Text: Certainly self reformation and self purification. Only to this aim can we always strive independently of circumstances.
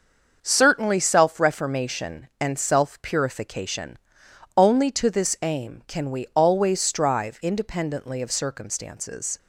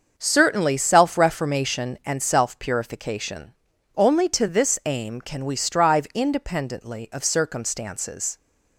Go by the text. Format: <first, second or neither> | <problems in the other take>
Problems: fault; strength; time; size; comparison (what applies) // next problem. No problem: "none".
first | starts louder than the rest; until 1.2 s; 6.5 dB; also in the first // skips "always"; at 5.5 s